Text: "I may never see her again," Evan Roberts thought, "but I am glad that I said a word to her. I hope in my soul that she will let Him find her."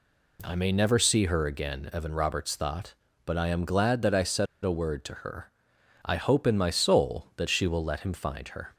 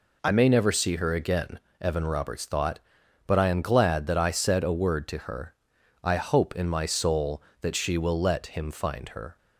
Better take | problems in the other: second | pauses between "said" and "a"; slight; at 4.4 s; 0.18 s long

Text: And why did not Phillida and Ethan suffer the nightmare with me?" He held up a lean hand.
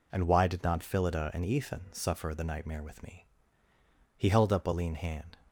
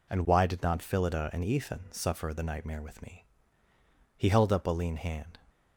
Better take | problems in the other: neither | none

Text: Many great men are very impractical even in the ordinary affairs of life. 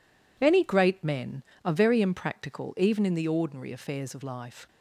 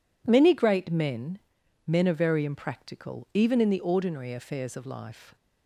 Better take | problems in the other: first | says "men" twice; at 1.8 s

